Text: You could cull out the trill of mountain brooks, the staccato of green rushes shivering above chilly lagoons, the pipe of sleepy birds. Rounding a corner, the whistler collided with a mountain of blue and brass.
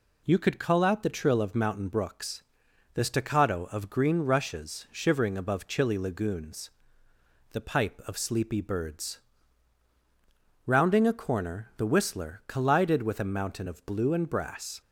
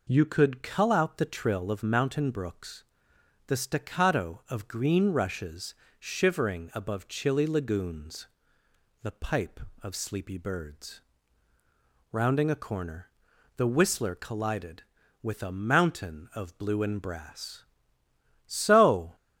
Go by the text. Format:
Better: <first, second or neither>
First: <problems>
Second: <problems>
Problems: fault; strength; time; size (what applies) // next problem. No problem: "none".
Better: first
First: none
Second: pauses between "rushes" and "shivering"; slight; at 5.7 s; 0.24 s long // goes on to say "So"; noticeable; from 18.4 s on; 0.70 s long